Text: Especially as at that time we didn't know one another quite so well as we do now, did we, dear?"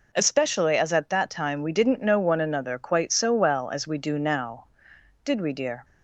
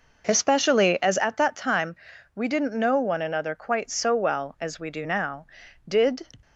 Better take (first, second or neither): first